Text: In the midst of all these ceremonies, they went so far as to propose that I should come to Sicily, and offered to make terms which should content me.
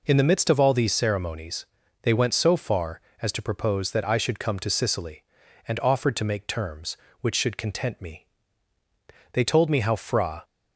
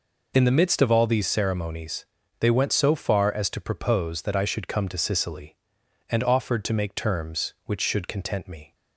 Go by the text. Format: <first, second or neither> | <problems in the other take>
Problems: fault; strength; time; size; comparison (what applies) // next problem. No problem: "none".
second | goes on to say "They told me how Fra"; noticeable; from 9.3 s on; 1.1 s long